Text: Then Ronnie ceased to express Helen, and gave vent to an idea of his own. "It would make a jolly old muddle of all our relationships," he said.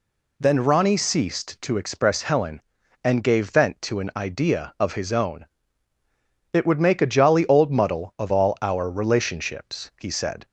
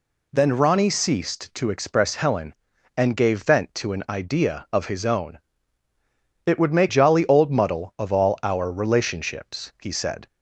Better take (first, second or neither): first